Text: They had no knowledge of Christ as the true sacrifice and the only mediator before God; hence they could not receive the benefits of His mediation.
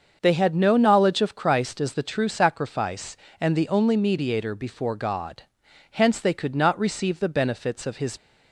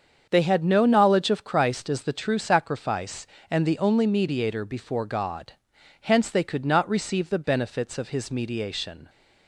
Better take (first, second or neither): second